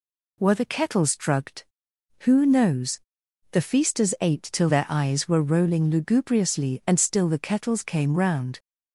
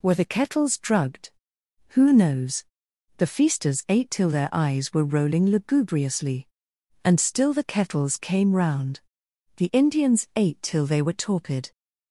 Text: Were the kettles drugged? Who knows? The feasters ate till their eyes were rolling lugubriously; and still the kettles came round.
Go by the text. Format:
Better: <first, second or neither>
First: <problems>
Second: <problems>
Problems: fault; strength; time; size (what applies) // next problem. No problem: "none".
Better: first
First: none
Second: goes on to say "The Indians ate till they were torpid"; strong; from 9.5 s on; 2.1 s long